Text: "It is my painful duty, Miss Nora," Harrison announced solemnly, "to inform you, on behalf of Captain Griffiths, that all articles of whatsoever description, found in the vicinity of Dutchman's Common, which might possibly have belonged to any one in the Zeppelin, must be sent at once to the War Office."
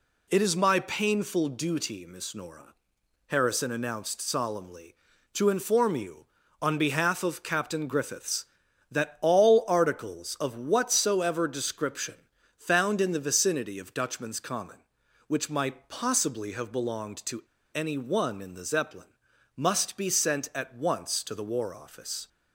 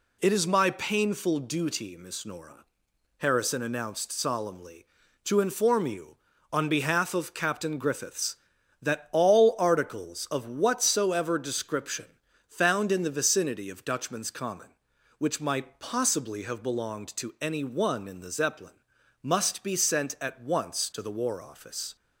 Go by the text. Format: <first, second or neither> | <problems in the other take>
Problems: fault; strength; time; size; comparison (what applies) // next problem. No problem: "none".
second | pauses between "to" and "any"; slight; at 17.4 s; 0.30 s long